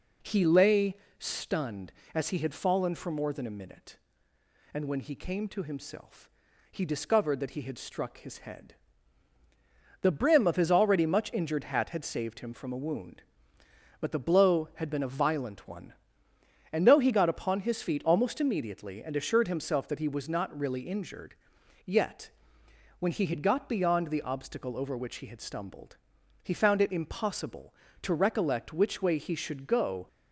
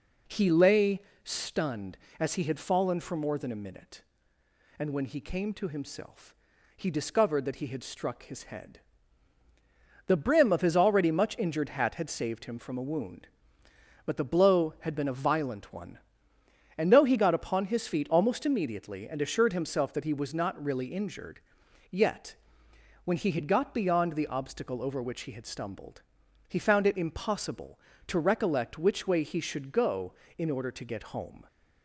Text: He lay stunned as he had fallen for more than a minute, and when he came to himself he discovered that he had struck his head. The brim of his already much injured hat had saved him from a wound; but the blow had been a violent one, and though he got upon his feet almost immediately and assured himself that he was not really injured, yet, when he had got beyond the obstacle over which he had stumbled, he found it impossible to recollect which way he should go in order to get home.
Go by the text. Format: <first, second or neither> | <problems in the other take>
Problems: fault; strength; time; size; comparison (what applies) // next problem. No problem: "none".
second | pauses between "lay" and "stunned"; slight; at 0.9 s; 0.22 s long; slight in the second // pauses between "himself" and "he"; at 6.2 s; 0.44 s long; also in the second // stops before "in order to get home"; at 30.0 s